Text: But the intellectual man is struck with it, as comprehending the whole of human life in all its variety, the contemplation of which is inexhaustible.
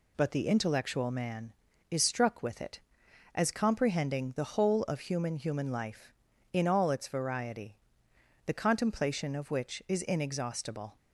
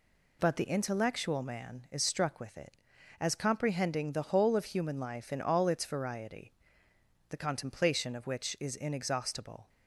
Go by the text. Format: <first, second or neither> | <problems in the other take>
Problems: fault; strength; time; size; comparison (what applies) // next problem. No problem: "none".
second | says "human" twice; at 5.3 s